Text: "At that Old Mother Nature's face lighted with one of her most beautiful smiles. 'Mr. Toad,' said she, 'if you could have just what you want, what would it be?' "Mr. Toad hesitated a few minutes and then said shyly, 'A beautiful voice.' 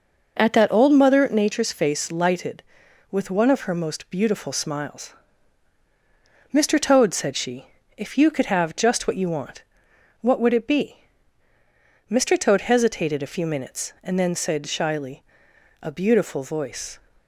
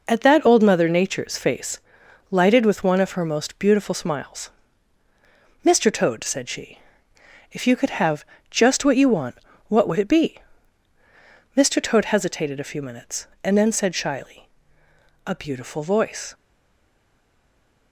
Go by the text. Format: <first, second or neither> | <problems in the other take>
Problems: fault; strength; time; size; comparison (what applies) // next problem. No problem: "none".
first | pauses between "face" and "lighted"; noticeable; at 1.7 s; 0.54 s long // pauses between "have" and "just"; slight; at 8.2 s; 0.24 s long // stays silent after the last word; noticeable; from 16.3 s on; 1.6 s long